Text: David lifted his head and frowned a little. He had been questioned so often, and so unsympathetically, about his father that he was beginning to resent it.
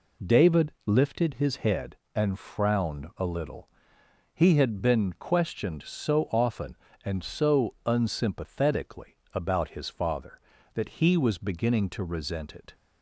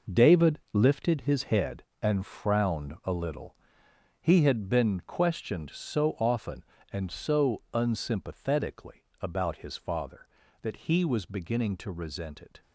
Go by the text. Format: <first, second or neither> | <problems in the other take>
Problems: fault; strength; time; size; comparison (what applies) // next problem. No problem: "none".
first | gets quieter; strong; throughout; 10 dB